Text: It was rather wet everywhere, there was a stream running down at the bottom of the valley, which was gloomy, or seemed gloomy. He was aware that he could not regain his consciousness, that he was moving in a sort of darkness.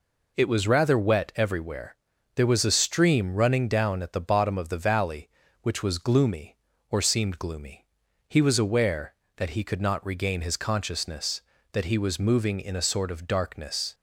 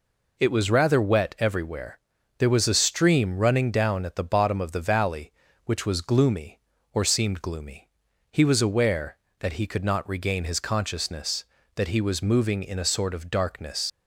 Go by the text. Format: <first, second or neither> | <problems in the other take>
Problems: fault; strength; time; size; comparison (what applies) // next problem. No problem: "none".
first | leaves "darkness" unfinished; at 13.8 s; 70 ms